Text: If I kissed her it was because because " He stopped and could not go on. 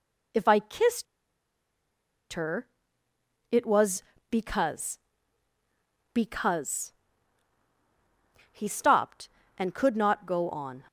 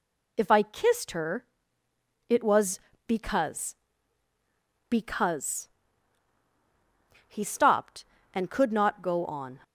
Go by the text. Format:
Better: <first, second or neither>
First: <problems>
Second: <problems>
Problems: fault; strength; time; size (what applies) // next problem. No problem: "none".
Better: second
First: pauses between "kissed" and "her"; strong; at 1.0 s; 1.2 s long // pauses between "her" and "it"; noticeable; at 2.6 s; 0.84 s long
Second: pauses between "her" and "it"; noticeable; at 1.4 s; 0.84 s long